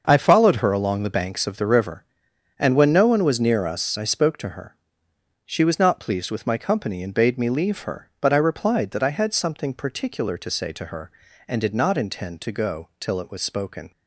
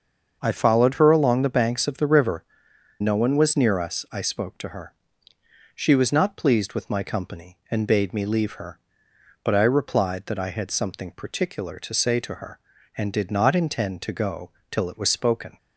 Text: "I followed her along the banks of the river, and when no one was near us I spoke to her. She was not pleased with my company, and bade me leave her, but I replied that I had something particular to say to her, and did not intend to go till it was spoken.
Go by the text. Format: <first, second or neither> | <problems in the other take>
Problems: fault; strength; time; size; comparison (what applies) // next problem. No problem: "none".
first | starts louder than the rest; until 1.4 s; 6.5 dB; also in the first // skips "and when"; at 2.7 s // pauses between "go" and "till"; slight; at 14.5 s; 0.20 s long